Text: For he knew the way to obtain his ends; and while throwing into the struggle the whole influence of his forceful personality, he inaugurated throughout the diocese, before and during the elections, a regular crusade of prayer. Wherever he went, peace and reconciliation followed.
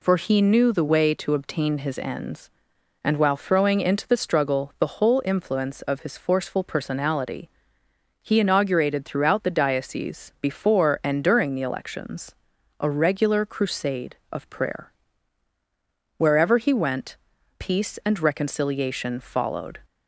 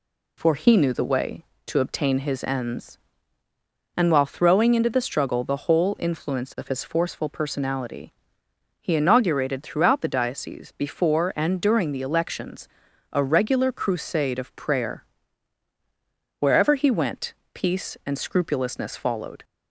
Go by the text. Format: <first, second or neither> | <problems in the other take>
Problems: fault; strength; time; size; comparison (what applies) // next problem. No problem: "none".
first | says "scrupulousness" for "reconciliation"; at 18.1 s